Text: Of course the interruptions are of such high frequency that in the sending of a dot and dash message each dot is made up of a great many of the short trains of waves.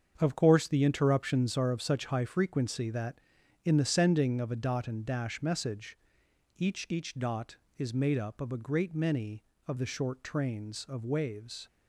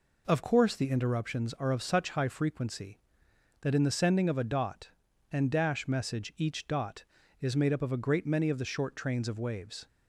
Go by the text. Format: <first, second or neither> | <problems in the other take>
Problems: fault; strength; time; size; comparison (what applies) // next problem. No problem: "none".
second | starts louder than the rest; strong; until 1.1 s; 7 dB // pauses between "message" and "each"; noticeable; at 5.9 s; 0.58 s long // says "each" twice; at 6.8 s